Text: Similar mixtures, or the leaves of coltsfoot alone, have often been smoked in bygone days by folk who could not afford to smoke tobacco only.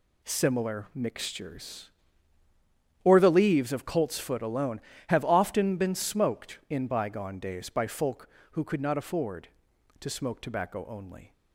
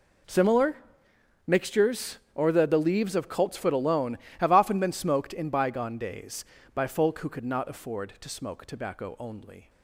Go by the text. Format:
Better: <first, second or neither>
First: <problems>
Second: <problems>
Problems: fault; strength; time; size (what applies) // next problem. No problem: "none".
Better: first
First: none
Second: pauses between "Similar" and "mixtures"; noticeable; at 0.7 s; 0.70 s long // says "the" twice; at 2.6 s